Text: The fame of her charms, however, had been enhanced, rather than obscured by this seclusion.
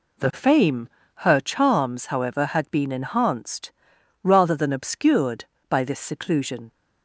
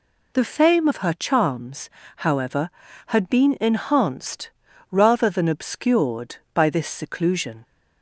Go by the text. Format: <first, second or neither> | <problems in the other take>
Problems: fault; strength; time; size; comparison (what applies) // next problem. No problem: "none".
second | skips "of"; at 1.0 s